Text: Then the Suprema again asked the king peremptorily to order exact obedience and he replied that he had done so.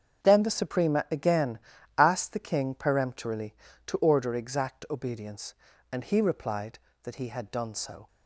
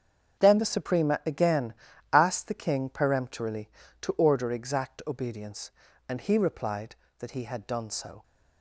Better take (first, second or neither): neither